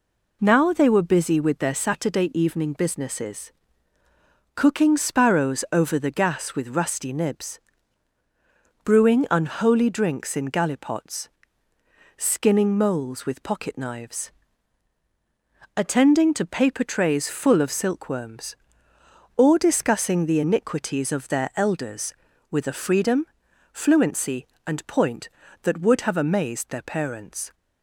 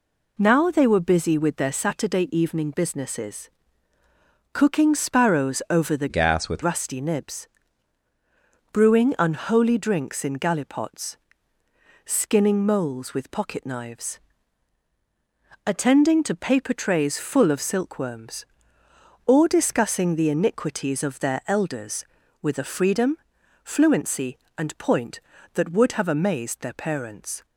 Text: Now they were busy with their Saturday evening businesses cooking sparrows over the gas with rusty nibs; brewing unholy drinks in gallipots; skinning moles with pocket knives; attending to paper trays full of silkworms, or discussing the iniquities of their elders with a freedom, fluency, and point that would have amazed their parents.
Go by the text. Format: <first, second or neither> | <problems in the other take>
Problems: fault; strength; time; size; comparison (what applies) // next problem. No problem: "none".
first | pauses between "businesses" and "cooking"; at 3.4 s; 1.0 s long; also in the first // changes voice from "gas" to "with"; from 6.0 to 6.6 s; 0.6 s long